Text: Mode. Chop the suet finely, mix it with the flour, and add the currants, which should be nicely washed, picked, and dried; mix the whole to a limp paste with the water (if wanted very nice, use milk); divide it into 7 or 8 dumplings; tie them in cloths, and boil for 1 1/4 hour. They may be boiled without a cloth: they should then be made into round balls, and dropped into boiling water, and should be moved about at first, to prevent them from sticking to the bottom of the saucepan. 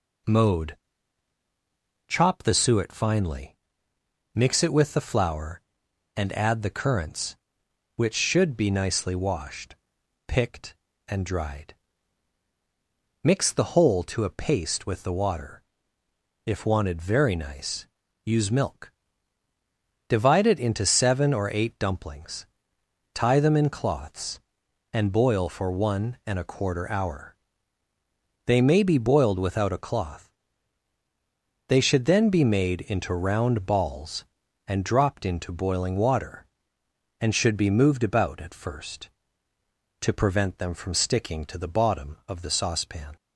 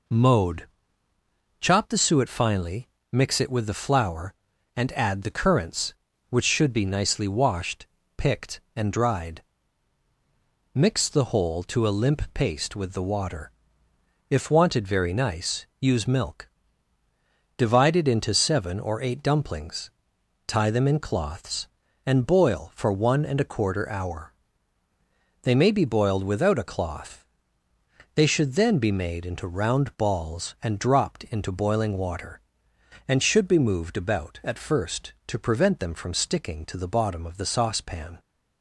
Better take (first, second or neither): second